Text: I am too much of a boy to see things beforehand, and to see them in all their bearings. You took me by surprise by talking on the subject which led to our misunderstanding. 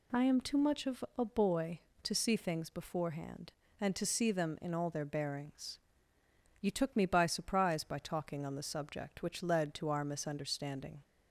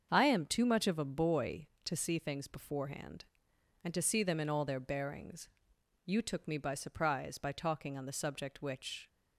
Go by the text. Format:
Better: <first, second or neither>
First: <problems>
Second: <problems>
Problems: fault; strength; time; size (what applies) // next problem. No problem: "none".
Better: first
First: none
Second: starts louder than the rest; until 1.1 s; 7 dB // stops before "led to our misunderstanding"; at 9.0 s